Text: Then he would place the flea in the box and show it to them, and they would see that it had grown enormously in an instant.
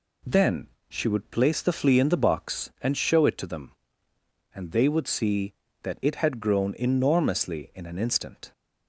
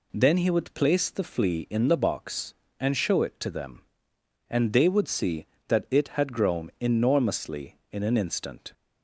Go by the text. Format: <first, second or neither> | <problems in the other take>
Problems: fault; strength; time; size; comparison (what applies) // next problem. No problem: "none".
second | says "she" for "he"; at 0.8 s